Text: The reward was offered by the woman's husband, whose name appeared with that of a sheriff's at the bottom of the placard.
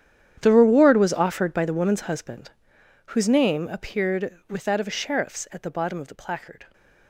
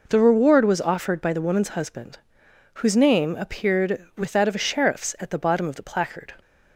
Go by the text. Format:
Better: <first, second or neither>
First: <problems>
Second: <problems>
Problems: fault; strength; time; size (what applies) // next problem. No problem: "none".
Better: second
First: gets quieter; strong; throughout; 17.5 dB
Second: none